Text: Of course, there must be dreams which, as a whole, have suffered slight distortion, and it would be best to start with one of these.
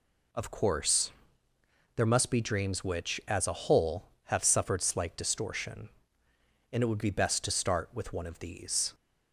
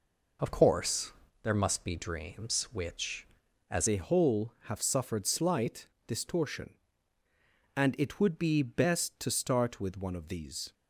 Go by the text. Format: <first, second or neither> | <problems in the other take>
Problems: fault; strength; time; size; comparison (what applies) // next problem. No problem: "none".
first | changes voice at "a"; from 3.8 s on; 6.9 s long // pauses between "slight" and "distortion"; slight; at 5.8 s; 0.20 s long